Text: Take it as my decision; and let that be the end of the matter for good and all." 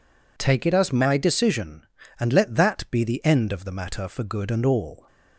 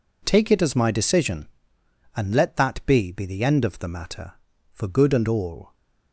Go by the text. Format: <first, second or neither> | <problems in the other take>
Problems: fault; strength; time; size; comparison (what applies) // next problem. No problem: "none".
first | says "be" twice; at 3.1 s